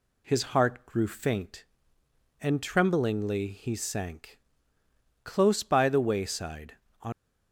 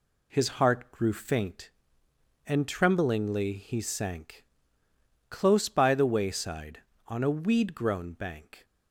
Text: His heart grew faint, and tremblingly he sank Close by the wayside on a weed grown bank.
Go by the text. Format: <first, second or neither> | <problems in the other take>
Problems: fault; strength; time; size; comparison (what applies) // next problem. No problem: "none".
second | pauses between "sank" and "Close"; noticeable; at 4.3 s; 0.84 s long; noticeable in the second // stops before "a weed grown bank"; at 7.1 s